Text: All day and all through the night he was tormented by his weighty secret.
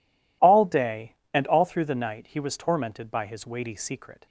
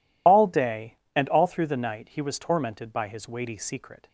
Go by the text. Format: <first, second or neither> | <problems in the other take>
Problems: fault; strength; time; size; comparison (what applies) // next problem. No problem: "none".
first | loses the start of "All"; at 0.2 s; 35 ms